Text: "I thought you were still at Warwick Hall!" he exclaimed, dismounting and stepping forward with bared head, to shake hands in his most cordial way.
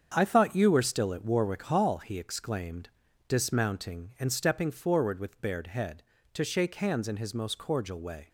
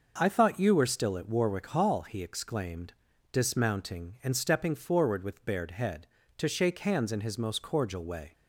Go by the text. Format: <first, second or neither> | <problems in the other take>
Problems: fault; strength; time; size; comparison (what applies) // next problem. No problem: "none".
second | gets quieter; strong; throughout; 7.5 dB